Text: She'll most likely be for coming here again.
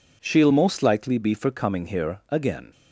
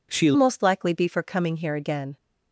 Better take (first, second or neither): first